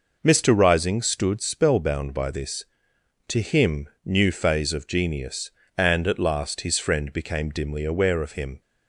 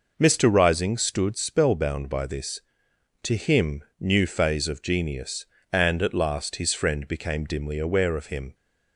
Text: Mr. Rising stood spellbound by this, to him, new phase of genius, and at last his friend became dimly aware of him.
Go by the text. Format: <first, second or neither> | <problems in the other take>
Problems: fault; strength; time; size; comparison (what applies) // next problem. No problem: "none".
neither | none